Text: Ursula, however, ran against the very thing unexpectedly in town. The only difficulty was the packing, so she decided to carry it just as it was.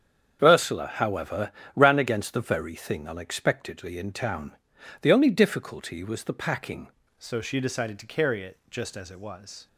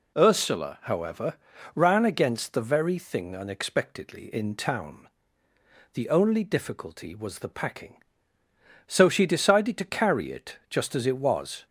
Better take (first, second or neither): second